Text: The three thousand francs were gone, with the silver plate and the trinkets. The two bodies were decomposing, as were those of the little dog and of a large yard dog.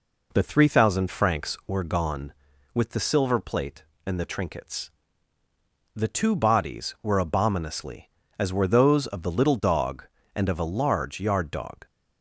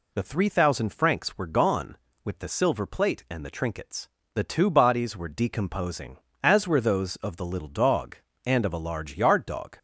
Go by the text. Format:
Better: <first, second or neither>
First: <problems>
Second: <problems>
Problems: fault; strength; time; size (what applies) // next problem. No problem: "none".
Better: second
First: says "abominously" for "decomposing"; at 7.1 s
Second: none